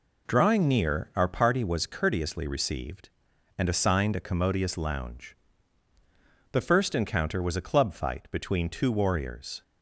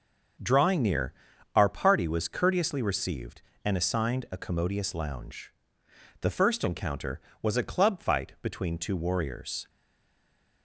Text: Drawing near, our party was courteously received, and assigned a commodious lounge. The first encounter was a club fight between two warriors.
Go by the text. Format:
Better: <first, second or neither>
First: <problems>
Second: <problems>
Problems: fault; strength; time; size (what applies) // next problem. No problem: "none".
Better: first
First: none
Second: starts louder than the rest; noticeable; until 1.8 s; 6 dB // stays silent after the last word; slight; from 9.6 s on; 1.0 s long